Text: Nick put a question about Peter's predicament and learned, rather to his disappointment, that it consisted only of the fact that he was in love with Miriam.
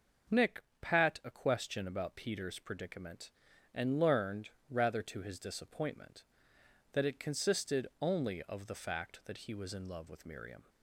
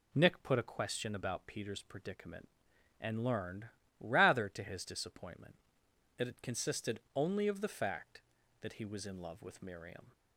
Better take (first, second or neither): second